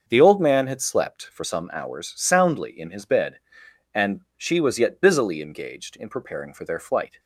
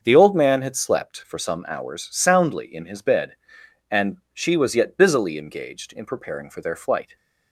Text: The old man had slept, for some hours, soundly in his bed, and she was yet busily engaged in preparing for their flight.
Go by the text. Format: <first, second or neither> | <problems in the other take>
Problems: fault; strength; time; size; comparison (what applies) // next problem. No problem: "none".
neither | starts louder than the rest; the same in both // pauses between "and" and "she"; slight; the same in both